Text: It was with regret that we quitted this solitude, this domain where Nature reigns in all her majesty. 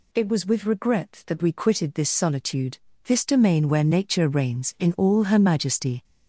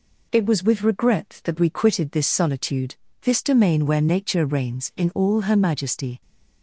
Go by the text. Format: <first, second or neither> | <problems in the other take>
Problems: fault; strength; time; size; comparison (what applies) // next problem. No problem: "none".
second | gets louder; noticeable; throughout; 4.5 dB